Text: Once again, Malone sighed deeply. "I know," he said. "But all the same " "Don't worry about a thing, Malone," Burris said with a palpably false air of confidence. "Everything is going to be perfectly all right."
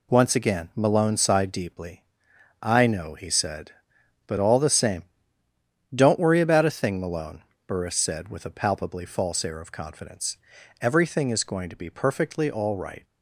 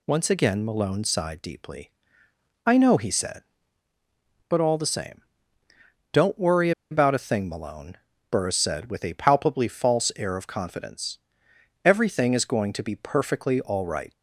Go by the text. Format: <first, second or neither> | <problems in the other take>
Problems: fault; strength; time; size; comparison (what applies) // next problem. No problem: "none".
first | pauses between "worry" and "about"; slight; at 6.7 s; 0.20 s long